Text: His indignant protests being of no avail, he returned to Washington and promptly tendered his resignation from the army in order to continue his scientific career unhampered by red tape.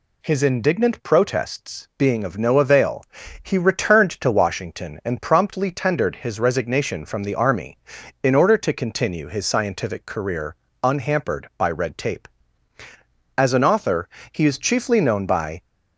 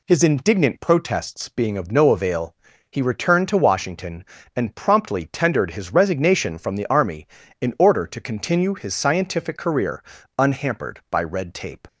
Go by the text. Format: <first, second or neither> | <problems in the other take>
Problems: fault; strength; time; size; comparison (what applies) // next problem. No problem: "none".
second | pauses between "career" and "unhampered"; slight; at 10.5 s; 0.28 s long; slight in the second // goes on to say "As an author he is chiefly known by"; strong; from 13.3 s on; 2.2 s long